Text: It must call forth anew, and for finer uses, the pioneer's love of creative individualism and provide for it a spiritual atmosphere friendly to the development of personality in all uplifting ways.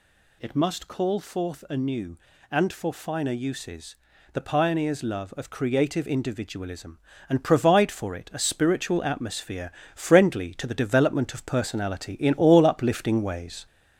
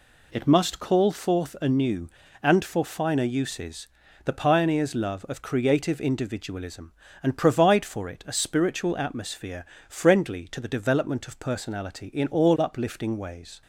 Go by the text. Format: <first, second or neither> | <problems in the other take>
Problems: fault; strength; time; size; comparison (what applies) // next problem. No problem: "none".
second | gets louder; throughout; 4 dB // pauses between "atmosphere" and "friendly"; slight; at 9.7 s; 0.24 s long; slight in the second